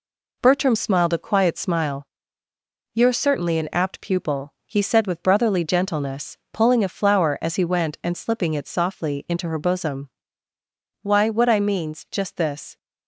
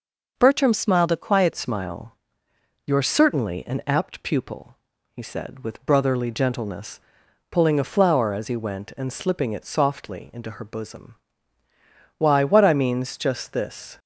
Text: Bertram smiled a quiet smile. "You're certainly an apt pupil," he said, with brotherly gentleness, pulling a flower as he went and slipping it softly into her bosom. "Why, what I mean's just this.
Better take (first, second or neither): first